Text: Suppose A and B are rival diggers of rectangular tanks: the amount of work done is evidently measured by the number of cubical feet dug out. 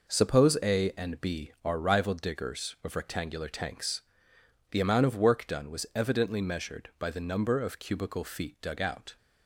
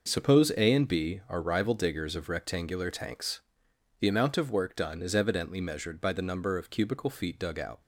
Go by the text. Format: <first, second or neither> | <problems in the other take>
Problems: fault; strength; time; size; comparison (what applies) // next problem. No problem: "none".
second | says "was" for "is"; at 5.7 s